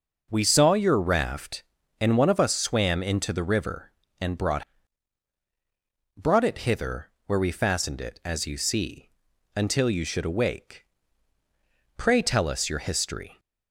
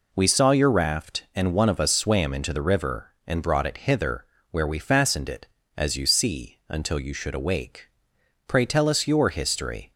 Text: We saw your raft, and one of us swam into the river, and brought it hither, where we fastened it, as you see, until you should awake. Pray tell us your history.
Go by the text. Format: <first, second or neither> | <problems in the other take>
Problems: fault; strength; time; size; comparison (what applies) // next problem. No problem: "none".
second | says "brought" twice; at 6.1 s